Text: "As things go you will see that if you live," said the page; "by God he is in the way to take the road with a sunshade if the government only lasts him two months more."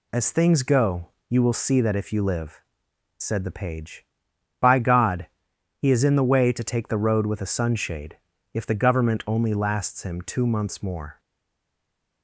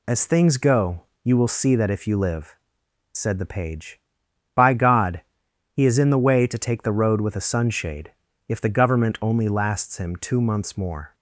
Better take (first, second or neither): second